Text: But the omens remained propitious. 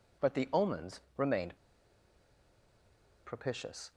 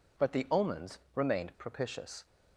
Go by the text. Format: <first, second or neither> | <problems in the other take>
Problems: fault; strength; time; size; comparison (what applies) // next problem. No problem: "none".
second | pauses between "omens" and "remained"; slight; at 0.9 s; 0.18 s long; slight in the second // pauses between "remained" and "propitious"; strong; at 1.5 s; 1.6 s long